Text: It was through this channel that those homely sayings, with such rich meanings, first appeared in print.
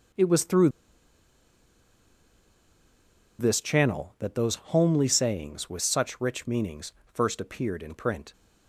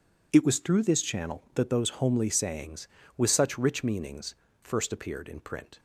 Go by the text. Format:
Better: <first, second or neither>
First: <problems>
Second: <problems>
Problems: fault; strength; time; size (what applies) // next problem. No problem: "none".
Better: second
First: starts louder than the rest; until 3.8 s; 6.5 dB // pauses between "through" and "this"; strong; at 0.6 s; 2.7 s long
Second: none